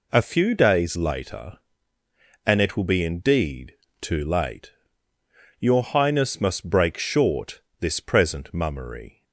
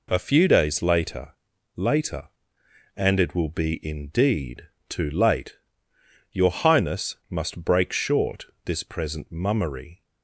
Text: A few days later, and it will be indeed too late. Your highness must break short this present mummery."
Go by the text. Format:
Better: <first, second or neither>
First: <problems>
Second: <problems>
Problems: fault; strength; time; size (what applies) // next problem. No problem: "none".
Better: first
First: pauses between "indeed" and "too"; slight; at 3.7 s; 0.26 s long // pauses between "short" and "this"; slight; at 7.5 s; 0.22 s long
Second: says "later" twice; at 1.7 s // pauses between "indeed" and "too"; slight; at 4.6 s; 0.26 s long // pauses between "short" and "this"; slight; at 8.4 s; 0.18 s long